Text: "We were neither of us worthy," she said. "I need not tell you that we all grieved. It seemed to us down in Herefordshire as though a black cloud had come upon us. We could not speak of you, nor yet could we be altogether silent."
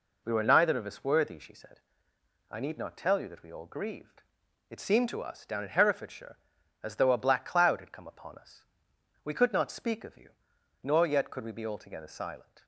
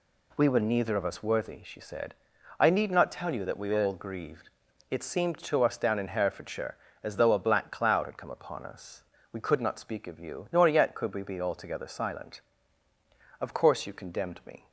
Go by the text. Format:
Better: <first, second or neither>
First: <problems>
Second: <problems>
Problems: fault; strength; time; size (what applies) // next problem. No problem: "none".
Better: first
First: none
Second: goes on to say "Of course you condemned me"; noticeable; from 13.4 s on; 1.2 s long